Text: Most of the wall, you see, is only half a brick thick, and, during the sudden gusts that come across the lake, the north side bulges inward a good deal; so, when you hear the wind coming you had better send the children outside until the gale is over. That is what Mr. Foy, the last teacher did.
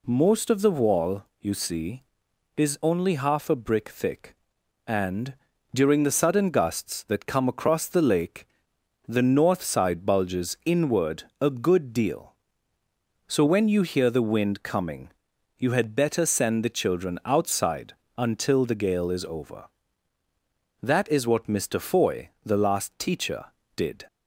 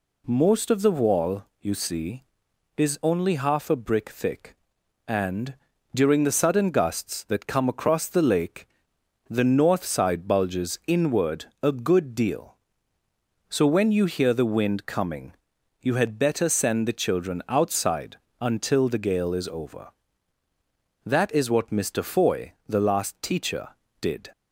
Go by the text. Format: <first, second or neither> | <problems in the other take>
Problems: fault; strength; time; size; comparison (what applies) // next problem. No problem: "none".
neither | pauses between "inward" and "a"; slight; the same in both // pauses between "coming" and "you"; noticeable; the same in both // pauses between "outside" and "until"; slight; the same in both